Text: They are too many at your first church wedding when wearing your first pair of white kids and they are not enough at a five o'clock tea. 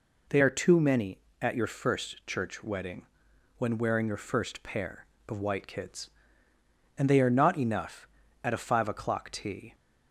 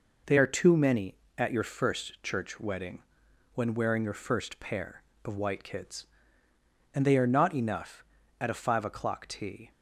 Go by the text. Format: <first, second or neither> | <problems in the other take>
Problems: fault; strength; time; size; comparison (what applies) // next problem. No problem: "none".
first | gets quieter; noticeable; throughout; 5.5 dB // pauses between "wedding" and "when"; noticeable; at 3.0 s; 0.54 s long; noticeable in the first